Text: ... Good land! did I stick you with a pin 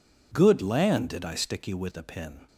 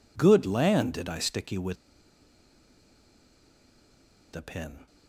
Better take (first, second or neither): first